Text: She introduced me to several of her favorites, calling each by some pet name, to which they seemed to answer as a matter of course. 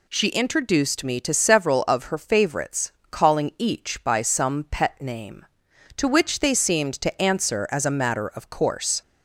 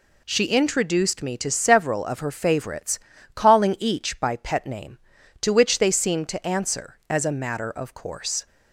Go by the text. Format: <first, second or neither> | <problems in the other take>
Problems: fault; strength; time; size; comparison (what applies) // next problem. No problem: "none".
first | skips "some"; at 4.3 s